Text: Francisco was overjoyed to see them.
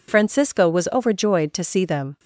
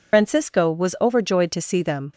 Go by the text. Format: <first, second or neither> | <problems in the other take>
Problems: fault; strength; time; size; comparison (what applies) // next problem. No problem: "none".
first | loses the start of "Francisco"; at 0.1 s; 70 ms